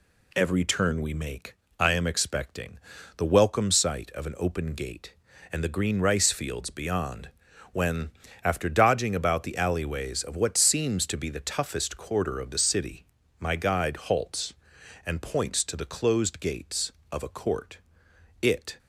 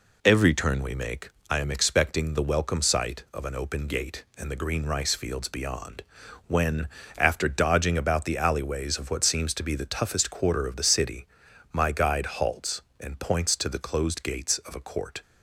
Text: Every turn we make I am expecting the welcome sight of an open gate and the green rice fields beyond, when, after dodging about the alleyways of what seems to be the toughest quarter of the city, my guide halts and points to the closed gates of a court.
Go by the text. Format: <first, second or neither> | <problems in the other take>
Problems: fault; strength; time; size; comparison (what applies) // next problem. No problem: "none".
second | pauses between "make" and "I"; slight; at 1.5 s; 0.22 s long; slight in the second // pauses between "expecting" and "the"; at 2.7 s; 0.40 s long // goes on to say "It"; slight; from 18.4 s on; 0.38 s long